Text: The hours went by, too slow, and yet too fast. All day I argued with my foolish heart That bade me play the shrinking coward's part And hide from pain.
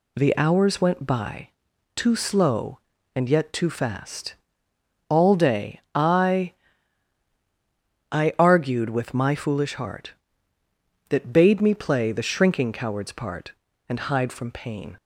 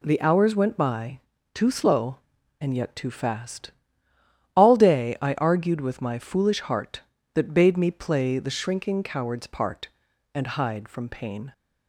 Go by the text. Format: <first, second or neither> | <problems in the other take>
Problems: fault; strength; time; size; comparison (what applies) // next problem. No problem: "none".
second | says "I" twice; at 8.1 s